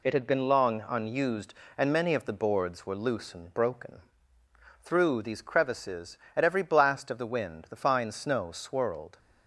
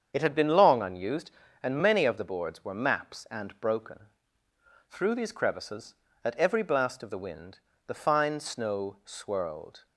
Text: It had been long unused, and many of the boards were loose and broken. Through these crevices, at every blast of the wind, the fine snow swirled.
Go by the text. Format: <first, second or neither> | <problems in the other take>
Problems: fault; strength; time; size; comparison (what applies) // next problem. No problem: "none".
first | starts louder than the rest; strong; until 1.1 s; 7.5 dB // says "maps" for "loose"; at 2.7 s